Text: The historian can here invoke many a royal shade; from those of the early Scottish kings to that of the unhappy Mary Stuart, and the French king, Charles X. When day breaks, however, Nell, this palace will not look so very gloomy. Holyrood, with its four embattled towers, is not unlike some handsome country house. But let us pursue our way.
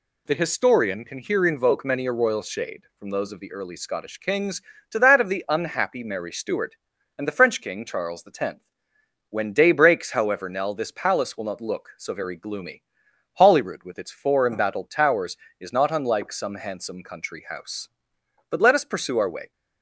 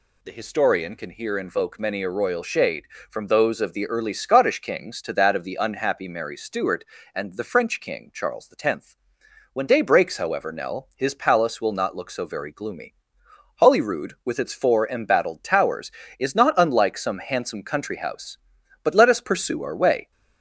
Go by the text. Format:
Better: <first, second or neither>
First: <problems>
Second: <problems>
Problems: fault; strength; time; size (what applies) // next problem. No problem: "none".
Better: first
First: none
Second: says "his" for "this"; at 10.9 s